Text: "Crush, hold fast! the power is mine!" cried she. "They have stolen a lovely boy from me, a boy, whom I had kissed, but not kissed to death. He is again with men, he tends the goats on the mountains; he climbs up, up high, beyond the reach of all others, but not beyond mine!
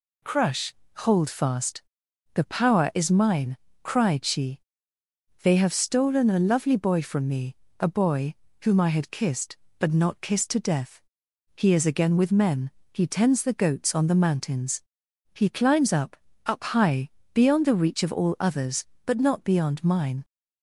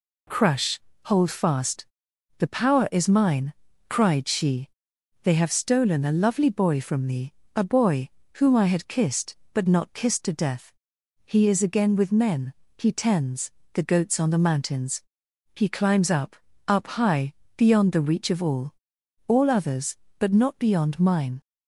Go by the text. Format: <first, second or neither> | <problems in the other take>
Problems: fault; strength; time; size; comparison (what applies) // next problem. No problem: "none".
first | pauses between "tends" and "the"; slight; at 13.5 s; 0.22 s long // says "all" twice; at 19.2 s